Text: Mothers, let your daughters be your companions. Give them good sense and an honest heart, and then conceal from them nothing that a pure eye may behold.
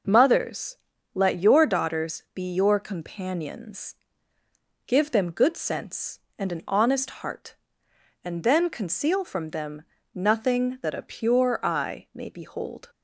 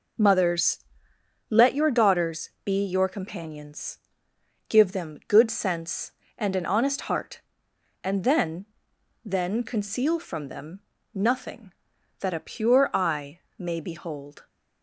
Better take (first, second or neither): first